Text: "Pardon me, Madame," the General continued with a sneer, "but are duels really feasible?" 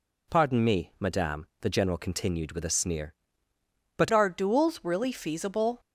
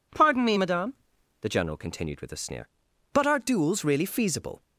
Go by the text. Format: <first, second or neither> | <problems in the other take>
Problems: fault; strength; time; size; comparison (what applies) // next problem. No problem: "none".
second | changes voice at "are"; from 4.1 s on; 1.6 s long